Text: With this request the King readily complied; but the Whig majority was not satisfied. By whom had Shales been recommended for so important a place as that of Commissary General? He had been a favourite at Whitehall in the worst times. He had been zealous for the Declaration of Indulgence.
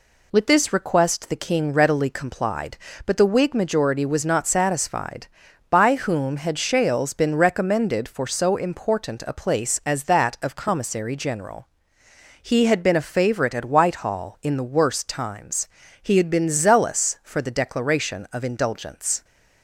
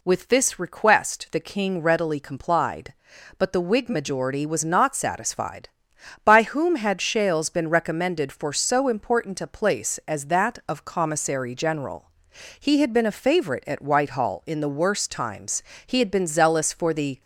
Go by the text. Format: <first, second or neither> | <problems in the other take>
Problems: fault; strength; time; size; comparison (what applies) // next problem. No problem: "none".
first | stops before "Declaration of Indulgence"; at 17.2 s